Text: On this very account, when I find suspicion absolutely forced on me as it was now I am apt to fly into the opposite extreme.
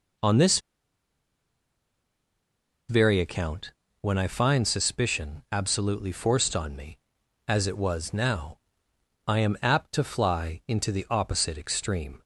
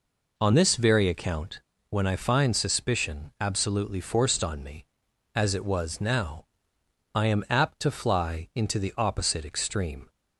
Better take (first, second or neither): second